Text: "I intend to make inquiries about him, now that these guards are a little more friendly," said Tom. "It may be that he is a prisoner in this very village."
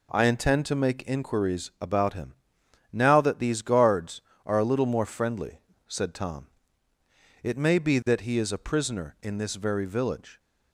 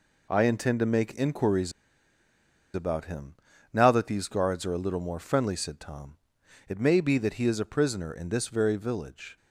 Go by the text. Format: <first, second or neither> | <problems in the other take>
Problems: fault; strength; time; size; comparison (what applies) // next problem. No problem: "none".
first | pauses between "inquiries" and "about"; at 1.7 s; 1.0 s long